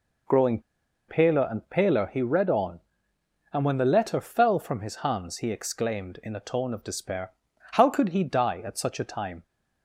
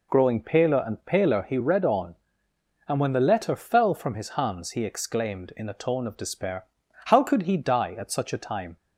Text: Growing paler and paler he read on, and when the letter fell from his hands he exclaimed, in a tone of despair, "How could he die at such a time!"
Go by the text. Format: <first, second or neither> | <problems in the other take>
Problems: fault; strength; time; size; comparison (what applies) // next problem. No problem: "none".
second | pauses between "Growing" and "paler"; noticeable; at 0.5 s; 0.49 s long